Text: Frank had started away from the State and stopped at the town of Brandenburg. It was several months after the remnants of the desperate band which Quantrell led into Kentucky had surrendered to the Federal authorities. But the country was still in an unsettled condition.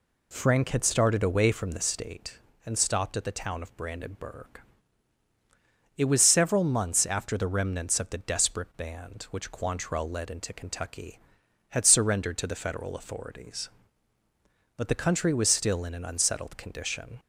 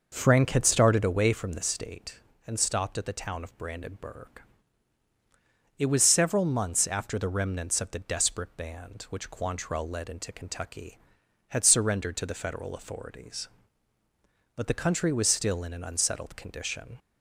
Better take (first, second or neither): first